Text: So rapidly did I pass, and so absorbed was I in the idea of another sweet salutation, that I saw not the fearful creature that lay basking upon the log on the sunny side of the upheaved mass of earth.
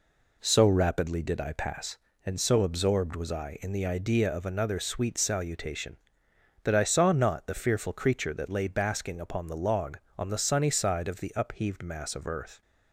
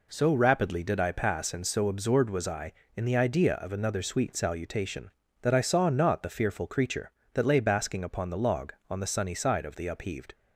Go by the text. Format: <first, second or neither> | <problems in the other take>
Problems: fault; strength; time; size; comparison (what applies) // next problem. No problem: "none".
first | stops before "mass of earth"; at 10.3 s